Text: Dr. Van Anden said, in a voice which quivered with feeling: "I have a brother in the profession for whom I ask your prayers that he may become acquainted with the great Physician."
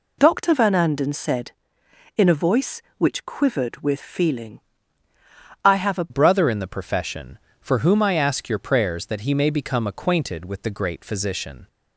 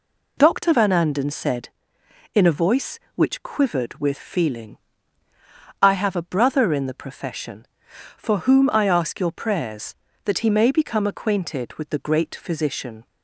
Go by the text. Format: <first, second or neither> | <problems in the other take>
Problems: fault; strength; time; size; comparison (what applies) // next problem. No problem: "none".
second | changes voice at "brother"; from 6.0 s on; 5.6 s long